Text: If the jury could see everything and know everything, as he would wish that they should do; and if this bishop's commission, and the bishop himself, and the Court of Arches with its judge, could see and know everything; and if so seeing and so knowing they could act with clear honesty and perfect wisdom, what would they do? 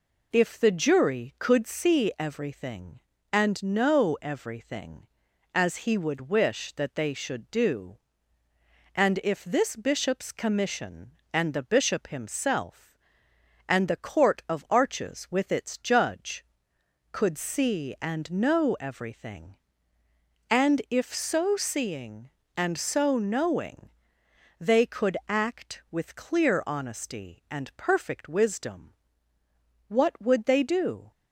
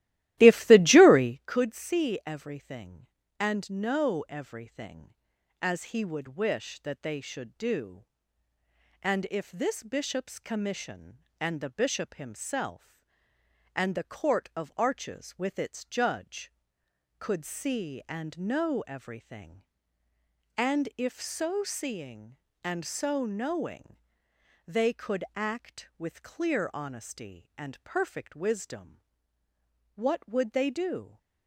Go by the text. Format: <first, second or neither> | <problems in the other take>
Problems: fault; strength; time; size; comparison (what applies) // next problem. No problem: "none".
first | starts louder than the rest; strong; until 1.4 s; 15.5 dB // pauses between "knowing" and "they"; noticeable; at 23.9 s; 0.72 s long; noticeable in the first